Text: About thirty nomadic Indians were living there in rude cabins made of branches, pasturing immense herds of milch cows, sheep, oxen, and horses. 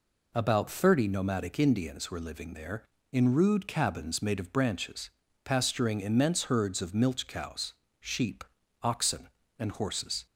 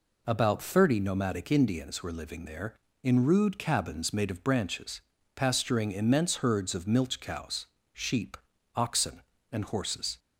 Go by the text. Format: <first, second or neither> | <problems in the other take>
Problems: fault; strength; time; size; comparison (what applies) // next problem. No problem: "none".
neither | none